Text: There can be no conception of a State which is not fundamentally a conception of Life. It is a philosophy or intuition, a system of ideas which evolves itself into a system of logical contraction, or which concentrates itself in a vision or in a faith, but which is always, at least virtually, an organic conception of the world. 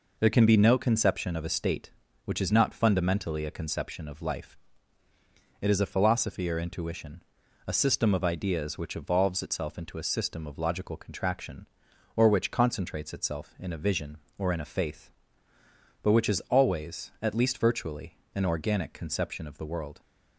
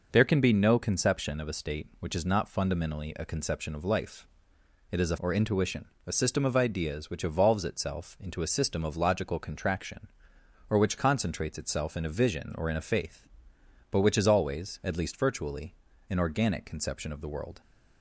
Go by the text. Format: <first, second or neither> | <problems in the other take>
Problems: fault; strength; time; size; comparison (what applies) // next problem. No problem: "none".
first | skips "philosophy"; at 5.1 s